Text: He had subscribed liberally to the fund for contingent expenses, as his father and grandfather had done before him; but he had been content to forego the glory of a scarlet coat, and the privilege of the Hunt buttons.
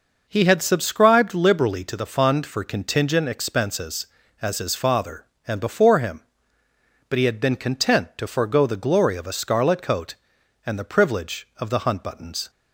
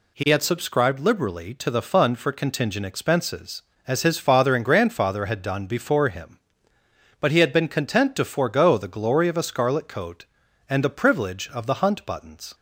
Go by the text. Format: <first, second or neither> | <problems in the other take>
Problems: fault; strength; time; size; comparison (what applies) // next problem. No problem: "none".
second | skips "grandfather had done"; at 5.5 s